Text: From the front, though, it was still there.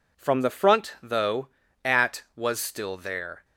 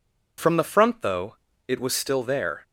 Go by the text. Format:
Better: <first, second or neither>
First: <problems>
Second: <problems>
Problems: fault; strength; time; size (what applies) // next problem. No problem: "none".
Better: second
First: says "at" for "it"; at 1.8 s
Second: none